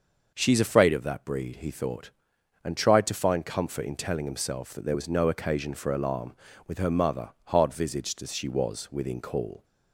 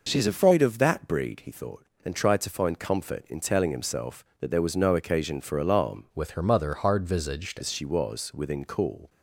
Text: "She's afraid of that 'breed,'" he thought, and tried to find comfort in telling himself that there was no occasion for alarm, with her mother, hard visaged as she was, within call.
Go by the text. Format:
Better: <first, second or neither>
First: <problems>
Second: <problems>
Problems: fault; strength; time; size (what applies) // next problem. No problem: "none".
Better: first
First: none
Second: changes voice from "with" to "visaged"; from 6.1 to 7.6 s; 1.5 s long